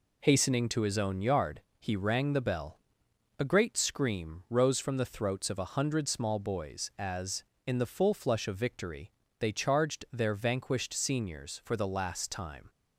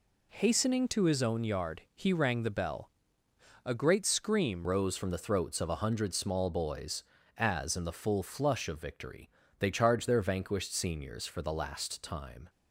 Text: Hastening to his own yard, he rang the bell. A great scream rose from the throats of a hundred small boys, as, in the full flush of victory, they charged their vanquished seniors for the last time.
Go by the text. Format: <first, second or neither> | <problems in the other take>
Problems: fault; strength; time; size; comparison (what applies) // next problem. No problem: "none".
first | changes voice at "rose"; from 4.6 s on; 7.8 s long